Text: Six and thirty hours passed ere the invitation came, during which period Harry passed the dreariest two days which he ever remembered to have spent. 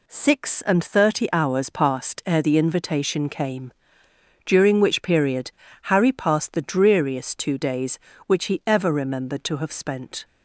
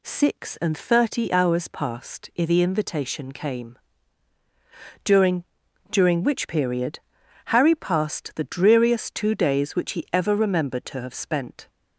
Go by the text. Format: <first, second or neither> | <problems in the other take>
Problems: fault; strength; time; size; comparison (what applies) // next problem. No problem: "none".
first | says "during" twice; at 5.9 s // pauses between "period" and "Harry"; noticeable; at 7.0 s; 0.46 s long; slight in the first